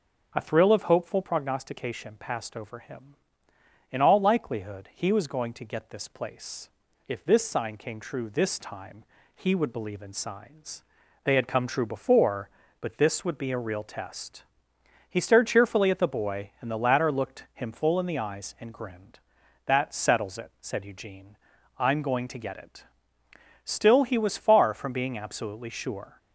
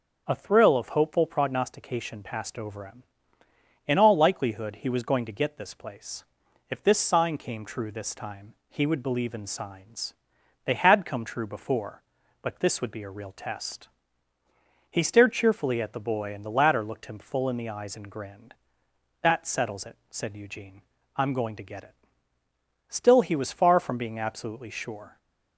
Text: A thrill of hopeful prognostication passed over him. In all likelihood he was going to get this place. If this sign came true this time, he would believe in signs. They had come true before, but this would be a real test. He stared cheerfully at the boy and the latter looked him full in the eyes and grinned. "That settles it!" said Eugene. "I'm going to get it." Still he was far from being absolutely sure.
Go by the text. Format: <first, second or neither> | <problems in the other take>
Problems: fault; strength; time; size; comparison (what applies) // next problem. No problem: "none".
neither | starts louder than the rest; the same in both